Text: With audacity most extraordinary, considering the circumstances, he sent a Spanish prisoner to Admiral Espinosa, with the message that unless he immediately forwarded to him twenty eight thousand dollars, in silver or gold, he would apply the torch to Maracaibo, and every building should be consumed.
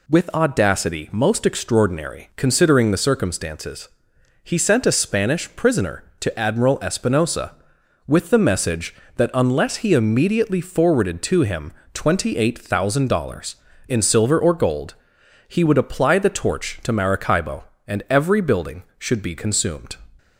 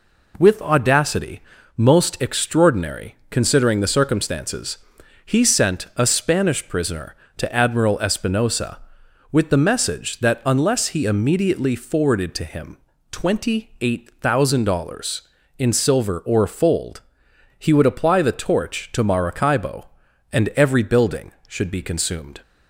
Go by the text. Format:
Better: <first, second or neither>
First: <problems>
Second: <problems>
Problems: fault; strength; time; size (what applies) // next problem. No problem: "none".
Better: first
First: pauses between "him" and "twenty"; slight; at 11.7 s; 0.20 s long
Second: pauses between "audacity" and "most"; slight; at 1.4 s; 0.36 s long // pauses between "him" and "twenty"; slight; at 12.7 s; 0.32 s long // says "fold" for "gold"; at 16.4 s